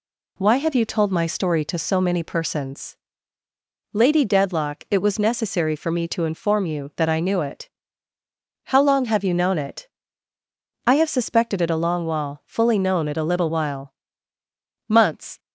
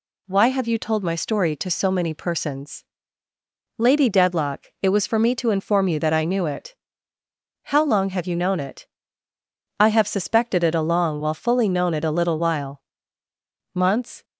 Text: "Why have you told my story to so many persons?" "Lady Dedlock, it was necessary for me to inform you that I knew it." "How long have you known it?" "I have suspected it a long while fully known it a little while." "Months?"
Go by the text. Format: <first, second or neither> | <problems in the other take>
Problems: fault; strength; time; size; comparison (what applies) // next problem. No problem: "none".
first | skips "necessary"; at 5.0 s